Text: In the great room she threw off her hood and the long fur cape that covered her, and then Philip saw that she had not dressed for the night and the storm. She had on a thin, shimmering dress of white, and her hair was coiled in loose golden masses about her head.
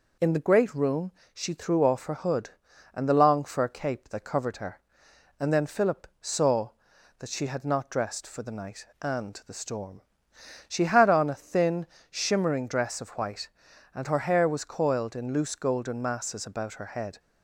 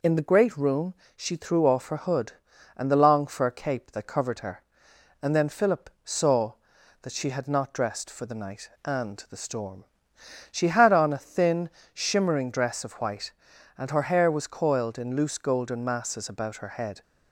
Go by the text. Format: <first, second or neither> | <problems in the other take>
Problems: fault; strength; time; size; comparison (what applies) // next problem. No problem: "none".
neither | pauses between "room" and "she"; slight; the same in both // pauses between "Philip" and "saw"; slight; the same in both